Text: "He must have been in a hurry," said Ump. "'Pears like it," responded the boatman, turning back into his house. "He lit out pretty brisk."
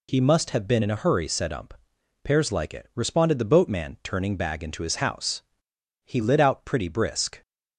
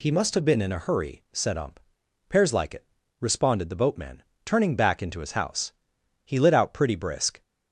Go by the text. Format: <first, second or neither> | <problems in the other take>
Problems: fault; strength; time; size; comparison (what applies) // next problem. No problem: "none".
second | says "bag" for "back"; at 4.3 s